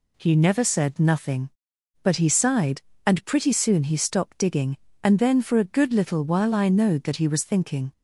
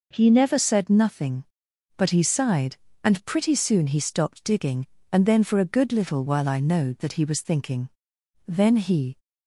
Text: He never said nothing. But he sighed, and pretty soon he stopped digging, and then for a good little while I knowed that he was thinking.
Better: first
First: none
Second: goes on to say "Then he"; noticeable; from 8.4 s on; 0.72 s long

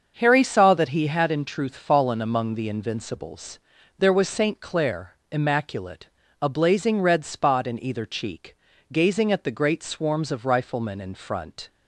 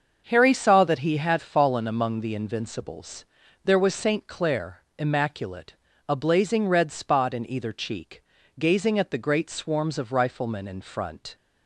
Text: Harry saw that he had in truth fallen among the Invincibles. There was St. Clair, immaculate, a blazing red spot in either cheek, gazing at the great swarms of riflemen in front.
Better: first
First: starts louder than the rest; until 1.1 s; 6.5 dB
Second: starts louder than the rest; until 1.2 s; 6.5 dB // skips "in truth"; at 1.3 s

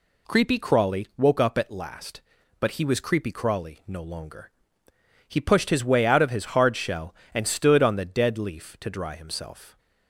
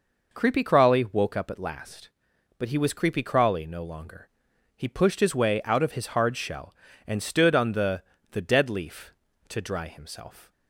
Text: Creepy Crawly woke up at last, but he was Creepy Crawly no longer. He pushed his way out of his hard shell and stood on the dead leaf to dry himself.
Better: first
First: none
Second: says "the" twice; at 8.3 s

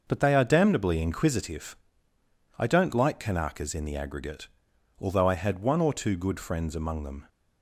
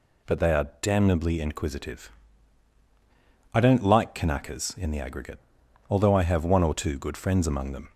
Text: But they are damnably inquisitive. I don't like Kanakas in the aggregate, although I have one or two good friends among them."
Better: second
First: starts louder than the rest; noticeable; until 1.0 s; 6 dB // says "had" for "have"; at 5.3 s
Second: none

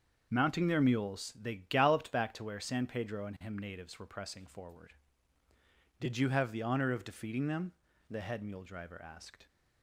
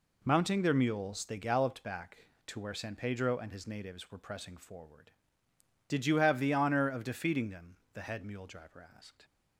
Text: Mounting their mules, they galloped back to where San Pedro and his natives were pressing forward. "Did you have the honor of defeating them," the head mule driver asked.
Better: second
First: starts louder than the rest; until 1.3 s; 6.5 dB // says "him" for "his"; at 3.4 s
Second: none

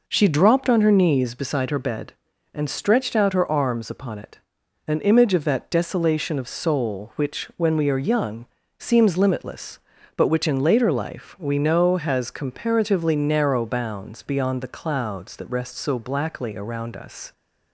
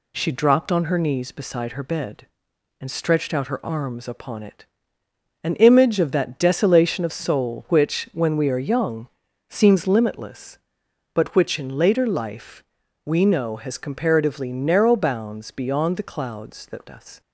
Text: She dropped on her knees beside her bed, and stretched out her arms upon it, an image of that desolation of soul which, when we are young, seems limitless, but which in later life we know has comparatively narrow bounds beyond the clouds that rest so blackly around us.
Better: first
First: none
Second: pauses between "life" and "we"; at 12.6 s; 0.40 s long // skips "rest so blackly around"; at 16.8 s

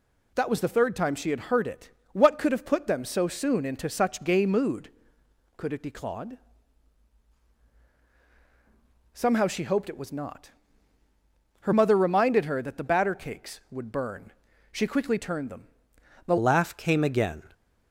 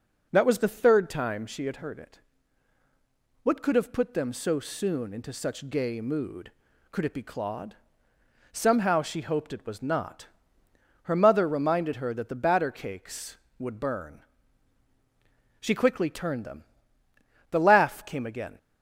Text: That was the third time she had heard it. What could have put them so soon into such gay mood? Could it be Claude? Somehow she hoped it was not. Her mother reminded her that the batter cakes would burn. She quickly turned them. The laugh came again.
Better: second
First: changes voice at "laugh"; from 16.3 s on; 1.1 s long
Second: none

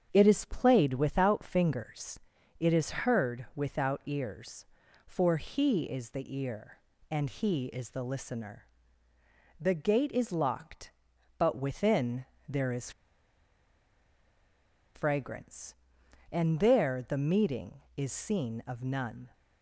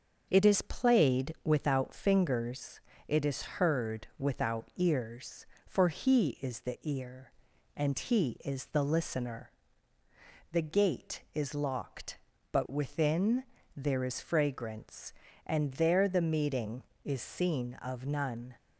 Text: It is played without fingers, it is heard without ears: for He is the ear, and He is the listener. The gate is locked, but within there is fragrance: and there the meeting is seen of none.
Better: second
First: starts louder than the rest; strong; until 1.1 s; 8 dB // pauses between "within" and "there"; slight; at 12.2 s; 0.24 s long // pauses between "is" and "fragrance"; strong; at 12.9 s; 2.0 s long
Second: starts louder than the rest; until 1.3 s; 6.5 dB // pauses between "within" and "there"; slight; at 13.4 s; 0.34 s long

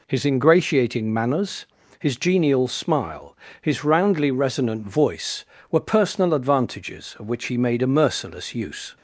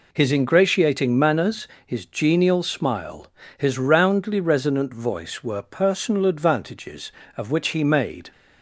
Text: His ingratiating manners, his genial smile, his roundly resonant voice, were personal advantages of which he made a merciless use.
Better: first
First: none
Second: stops before "a merciless use"; at 8.3 s

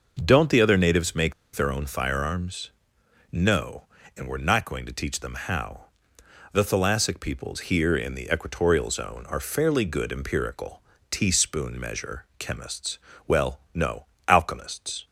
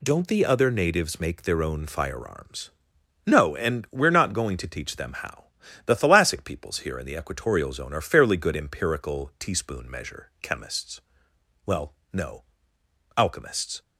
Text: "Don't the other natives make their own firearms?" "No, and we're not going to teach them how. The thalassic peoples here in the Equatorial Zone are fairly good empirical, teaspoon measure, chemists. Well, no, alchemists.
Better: second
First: pauses between "make" and "their"; slight; at 1.3 s; 0.22 s long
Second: none

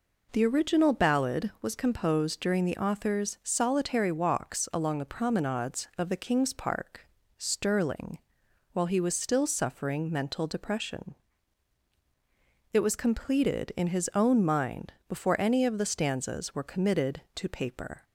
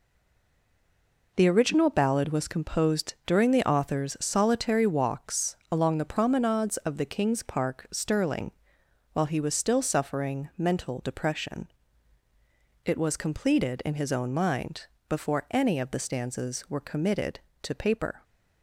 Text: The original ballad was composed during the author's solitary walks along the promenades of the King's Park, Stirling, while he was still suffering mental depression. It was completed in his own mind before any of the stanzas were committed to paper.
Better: first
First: pauses between "mind" and "before"; slight; at 14.9 s; 0.16 s long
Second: stays silent before the first word; noticeable; until 1.3 s; 1.3 s long // pauses between "walks" and "along"; slight; at 5.5 s; 0.16 s long // pauses between "mind" and "before"; slight; at 14.8 s; 0.24 s long

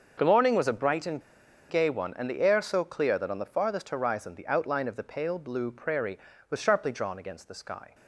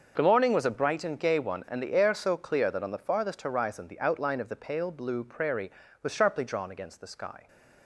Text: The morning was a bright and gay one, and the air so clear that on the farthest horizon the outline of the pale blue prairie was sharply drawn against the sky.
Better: second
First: starts louder than the rest; until 1.1 s; 6.5 dB // pauses between "and" and "gay"; noticeable; at 1.2 s; 0.49 s long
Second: starts louder than the rest; until 1.1 s; 6.5 dB

